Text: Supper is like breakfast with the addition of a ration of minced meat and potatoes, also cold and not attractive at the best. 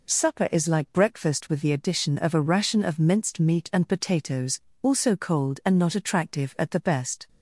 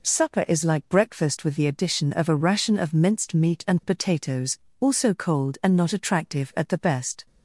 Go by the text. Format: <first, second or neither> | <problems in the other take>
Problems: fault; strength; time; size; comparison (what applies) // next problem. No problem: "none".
neither | none